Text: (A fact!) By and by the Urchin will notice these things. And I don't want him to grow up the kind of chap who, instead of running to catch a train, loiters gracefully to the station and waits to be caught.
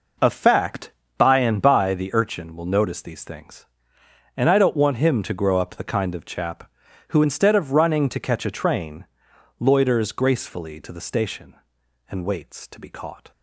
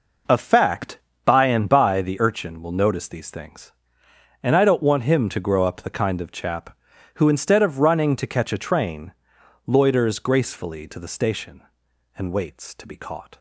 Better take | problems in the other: neither | none

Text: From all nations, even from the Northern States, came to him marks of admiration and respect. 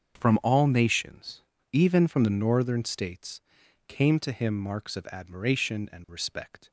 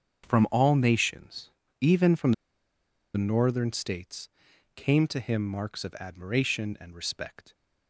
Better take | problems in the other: first | starts louder than the rest; until 1.3 s; 7 dB; also in the first // pauses between "from" and "the"; noticeable; at 2.3 s; 0.81 s long

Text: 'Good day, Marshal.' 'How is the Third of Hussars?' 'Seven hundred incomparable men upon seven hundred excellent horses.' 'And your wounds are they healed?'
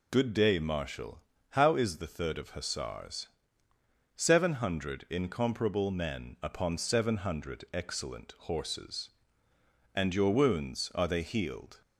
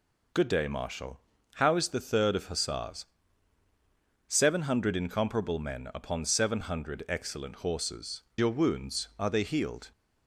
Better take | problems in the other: first | skips "And"; at 8.3 s

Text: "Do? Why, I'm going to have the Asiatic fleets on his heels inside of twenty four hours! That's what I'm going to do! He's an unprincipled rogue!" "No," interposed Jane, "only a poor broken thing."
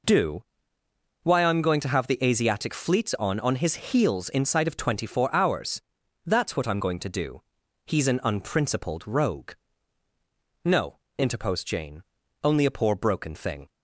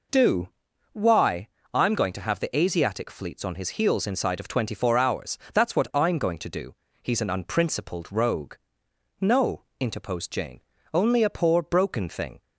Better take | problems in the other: second | says "on" twice; at 3.3 s

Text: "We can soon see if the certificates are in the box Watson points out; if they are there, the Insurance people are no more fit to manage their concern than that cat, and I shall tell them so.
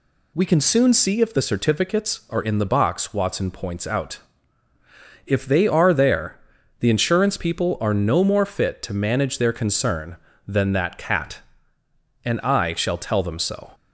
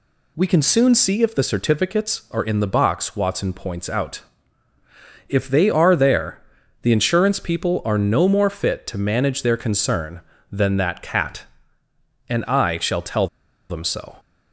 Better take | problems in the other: first | pauses between "tell" and "them"; at 13.2 s; 0.41 s long

